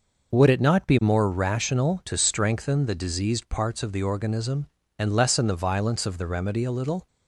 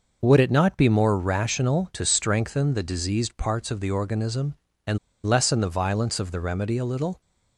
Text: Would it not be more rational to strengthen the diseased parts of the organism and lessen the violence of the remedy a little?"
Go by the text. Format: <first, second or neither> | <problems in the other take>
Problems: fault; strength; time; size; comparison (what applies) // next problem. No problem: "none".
first | pauses between "and" and "lessen"; slight; at 4.9 s; 0.28 s long